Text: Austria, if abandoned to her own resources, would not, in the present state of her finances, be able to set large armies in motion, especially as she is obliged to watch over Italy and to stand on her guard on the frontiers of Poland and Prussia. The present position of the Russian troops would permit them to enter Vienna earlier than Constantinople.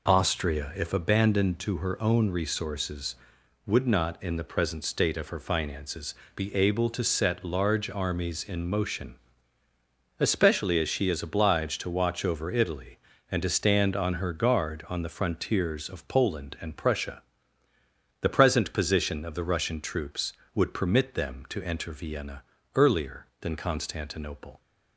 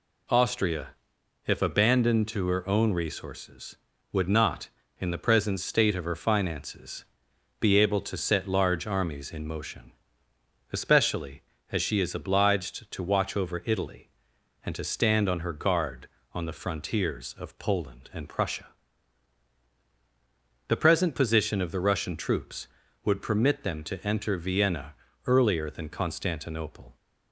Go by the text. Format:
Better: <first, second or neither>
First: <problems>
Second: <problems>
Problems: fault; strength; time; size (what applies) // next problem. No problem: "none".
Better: neither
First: pauses between "Vienna" and "earlier"; slight; at 22.4 s; 0.32 s long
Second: pauses between "Vienna" and "earlier"; slight; at 24.9 s; 0.32 s long